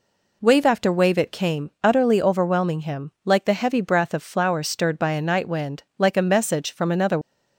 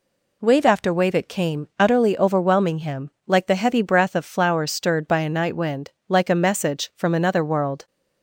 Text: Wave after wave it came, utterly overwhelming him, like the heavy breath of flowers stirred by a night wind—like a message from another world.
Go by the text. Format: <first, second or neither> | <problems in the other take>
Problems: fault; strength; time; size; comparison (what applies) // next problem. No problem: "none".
second | stops before "world"; at 7.2 s